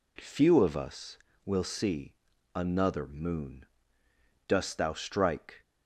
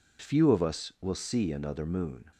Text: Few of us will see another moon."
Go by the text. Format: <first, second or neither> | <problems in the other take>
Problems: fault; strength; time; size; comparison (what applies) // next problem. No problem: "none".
second | pauses between "see" and "another"; at 2.1 s; 0.40 s long // goes on to say "Dost thou strike"; noticeable; from 4.4 s on; 1.1 s long